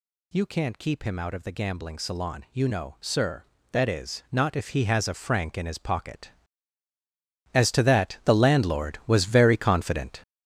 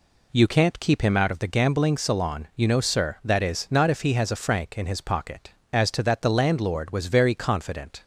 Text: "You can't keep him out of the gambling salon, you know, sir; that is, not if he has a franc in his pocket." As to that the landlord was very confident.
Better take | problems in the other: second | gets louder; strong; throughout; 8.5 dB

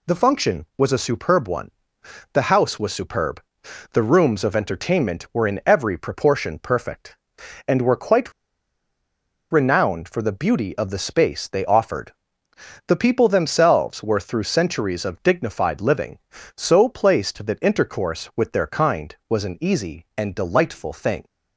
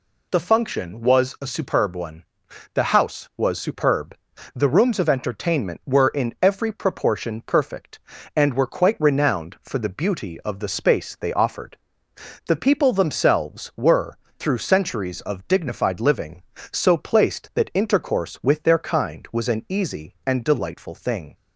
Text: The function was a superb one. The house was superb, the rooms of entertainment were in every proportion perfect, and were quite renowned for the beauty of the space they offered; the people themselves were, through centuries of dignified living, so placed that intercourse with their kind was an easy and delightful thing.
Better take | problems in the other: second | pauses between "quite" and "renowned"; at 8.3 s; 1.1 s long

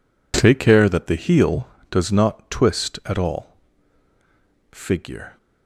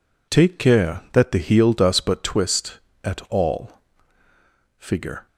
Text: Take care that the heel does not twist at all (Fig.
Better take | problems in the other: first | says "but" for "not"; at 1.9 s

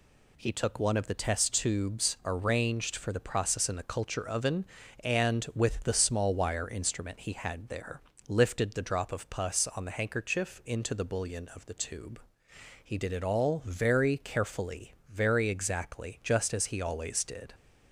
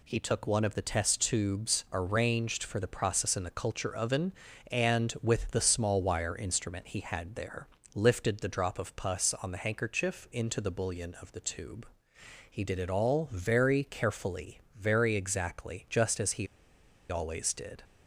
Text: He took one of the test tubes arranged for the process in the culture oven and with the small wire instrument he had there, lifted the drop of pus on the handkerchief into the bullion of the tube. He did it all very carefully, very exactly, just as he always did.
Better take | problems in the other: first | pauses between "he" and "always"; noticeable; at 16.4 s; 0.64 s long

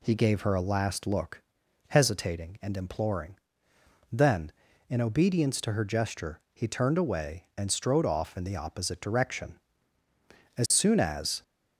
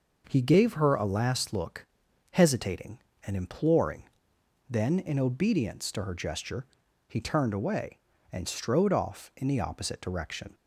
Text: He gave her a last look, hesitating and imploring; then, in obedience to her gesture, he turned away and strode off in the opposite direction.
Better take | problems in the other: second | goes on to say "As soon as"; noticeable; from 10.5 s on; 0.85 s long

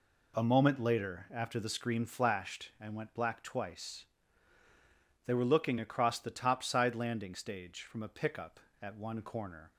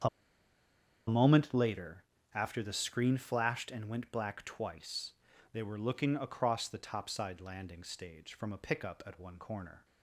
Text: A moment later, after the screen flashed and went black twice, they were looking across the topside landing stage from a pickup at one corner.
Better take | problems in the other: first | starts louder than the rest; strong; until 2.3 s; 7.5 dB // pauses between "A" and "moment"; at 0.0 s; 0.99 s long

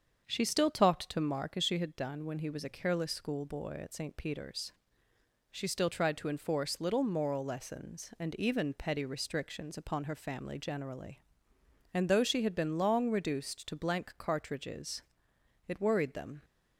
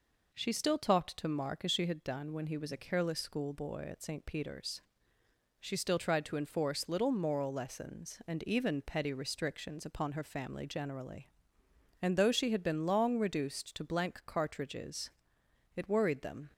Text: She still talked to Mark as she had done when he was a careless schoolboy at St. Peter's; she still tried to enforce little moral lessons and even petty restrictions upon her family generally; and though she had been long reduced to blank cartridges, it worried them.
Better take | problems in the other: second | starts louder than the rest; until 1.5 s; 7 dB

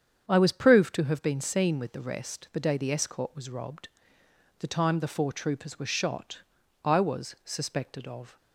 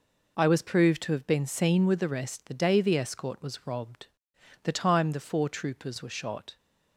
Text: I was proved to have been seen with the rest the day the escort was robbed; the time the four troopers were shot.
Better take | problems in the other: second | starts louder than the rest; strong; until 1.3 s; 8 dB // goes on to say "I was suspected of"; from 6.8 s on; 1.5 s long

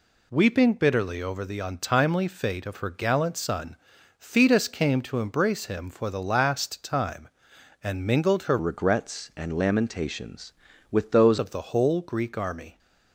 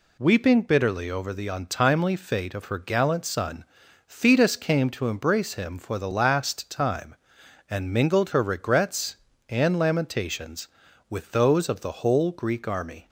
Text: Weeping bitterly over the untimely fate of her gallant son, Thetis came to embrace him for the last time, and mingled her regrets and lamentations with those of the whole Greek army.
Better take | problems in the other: second | changes voice from "regrets" to "those"; from 8.5 to 11.3 s; 2.8 s long

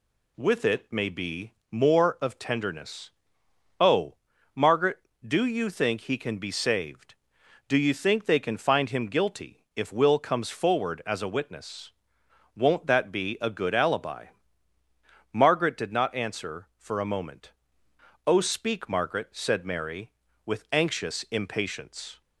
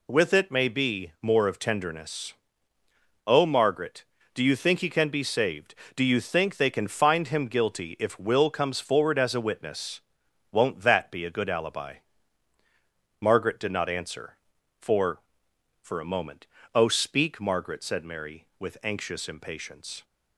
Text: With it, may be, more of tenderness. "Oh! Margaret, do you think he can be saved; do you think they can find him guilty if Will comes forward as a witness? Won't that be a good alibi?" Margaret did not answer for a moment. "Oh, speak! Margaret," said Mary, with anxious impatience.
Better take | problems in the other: first | says "for" twice; at 15.8 s

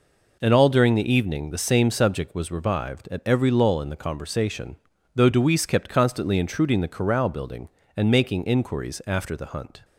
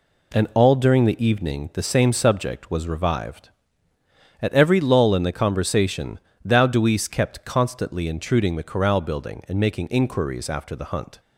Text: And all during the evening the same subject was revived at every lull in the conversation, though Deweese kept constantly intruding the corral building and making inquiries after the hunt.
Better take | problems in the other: first | says "thou" for "though"; at 6.4 s

